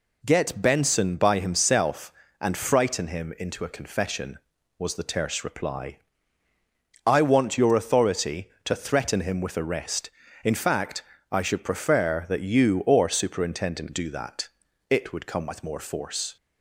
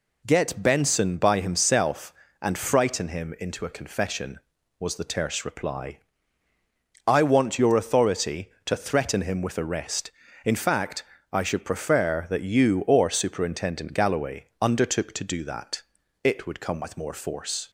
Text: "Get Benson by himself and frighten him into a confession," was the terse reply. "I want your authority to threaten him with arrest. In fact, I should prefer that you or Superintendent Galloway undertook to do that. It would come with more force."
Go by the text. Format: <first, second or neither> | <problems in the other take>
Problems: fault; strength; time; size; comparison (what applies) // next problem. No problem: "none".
second | skips "Galloway undertook to"; at 13.9 s